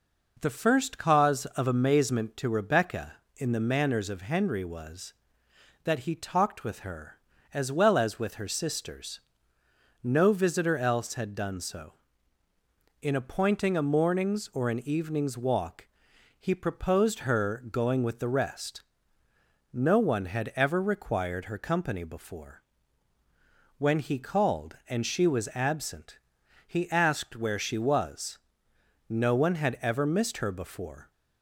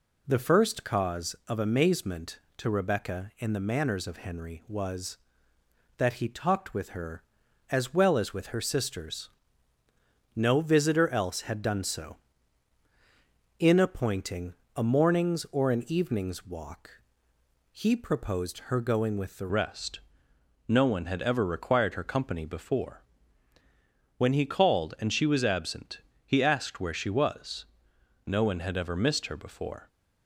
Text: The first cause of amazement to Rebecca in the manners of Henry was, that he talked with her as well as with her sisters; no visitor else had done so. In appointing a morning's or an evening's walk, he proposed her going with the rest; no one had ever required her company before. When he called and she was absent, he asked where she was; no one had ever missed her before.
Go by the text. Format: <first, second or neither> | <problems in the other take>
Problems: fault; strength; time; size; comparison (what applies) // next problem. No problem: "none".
first | pauses between "appointing" and "a"; slight; at 14.5 s; 0.22 s long // changes voice at "rest"; from 19.4 s on; 10.4 s long